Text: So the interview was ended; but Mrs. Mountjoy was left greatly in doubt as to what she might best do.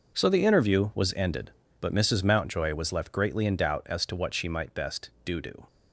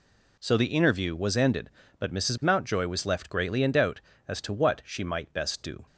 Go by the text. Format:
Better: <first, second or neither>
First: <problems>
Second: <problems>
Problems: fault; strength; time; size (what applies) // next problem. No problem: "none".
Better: second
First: says "do" twice; at 5.4 s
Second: none